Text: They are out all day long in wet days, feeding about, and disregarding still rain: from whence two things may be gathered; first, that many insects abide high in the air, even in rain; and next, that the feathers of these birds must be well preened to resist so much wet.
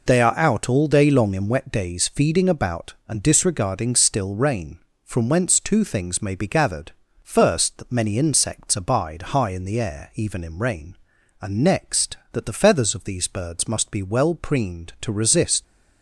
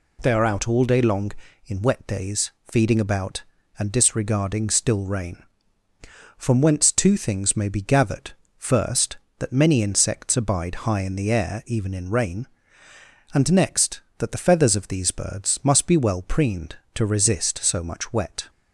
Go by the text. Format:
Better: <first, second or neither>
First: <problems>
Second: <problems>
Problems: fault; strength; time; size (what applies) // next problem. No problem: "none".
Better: second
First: stops before "so much wet"; at 15.6 s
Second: none